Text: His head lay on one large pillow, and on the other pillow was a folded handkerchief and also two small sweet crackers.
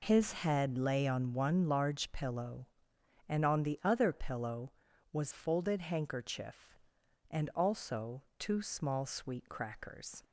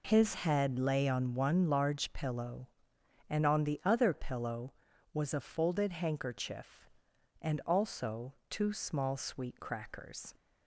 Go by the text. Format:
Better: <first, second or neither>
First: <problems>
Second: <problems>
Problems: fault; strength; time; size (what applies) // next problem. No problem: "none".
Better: second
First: skips "a"; at 5.3 s // pauses between "also" and "two"; slight; at 8.2 s; 0.16 s long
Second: pauses between "also" and "two"; slight; at 8.3 s; 0.16 s long